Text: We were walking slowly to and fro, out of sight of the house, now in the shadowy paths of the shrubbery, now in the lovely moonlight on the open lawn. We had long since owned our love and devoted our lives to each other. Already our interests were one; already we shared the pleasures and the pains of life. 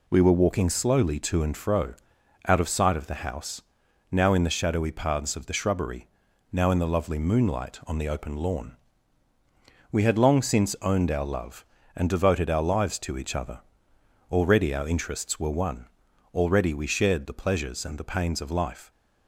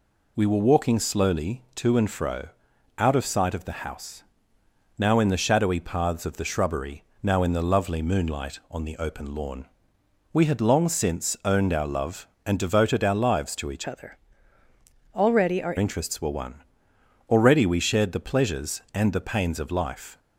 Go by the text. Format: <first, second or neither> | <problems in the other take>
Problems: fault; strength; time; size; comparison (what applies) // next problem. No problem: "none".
first | changes voice from "other" to "our"; from 13.8 to 15.7 s; 1.9 s long